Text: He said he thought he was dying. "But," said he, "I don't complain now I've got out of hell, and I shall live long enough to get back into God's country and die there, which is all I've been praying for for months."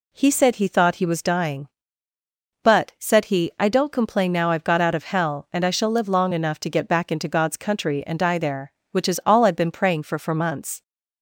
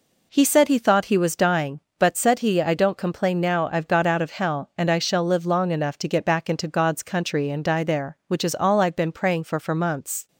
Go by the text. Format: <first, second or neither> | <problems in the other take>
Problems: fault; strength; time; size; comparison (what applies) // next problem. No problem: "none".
neither | none